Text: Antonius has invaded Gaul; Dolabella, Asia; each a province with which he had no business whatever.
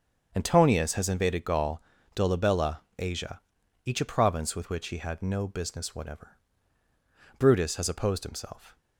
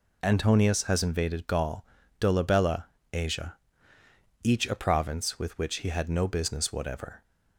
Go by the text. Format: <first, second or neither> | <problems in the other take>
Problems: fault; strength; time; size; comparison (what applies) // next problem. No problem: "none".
second | starts louder than the rest; until 1.3 s; 7 dB // goes on to say "Brutus has opposed himself"; from 7.3 s on; 1.3 s long